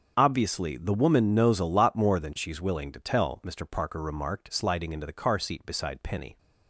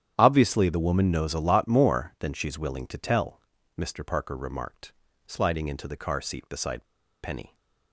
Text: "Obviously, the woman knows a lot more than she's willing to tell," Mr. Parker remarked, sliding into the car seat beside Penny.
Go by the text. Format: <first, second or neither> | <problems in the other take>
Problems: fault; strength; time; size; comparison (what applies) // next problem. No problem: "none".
first | starts louder than the rest; strong; until 1.1 s; 10 dB; also in the first // pauses between "beside" and "Penny"; at 6.8 s; 0.37 s long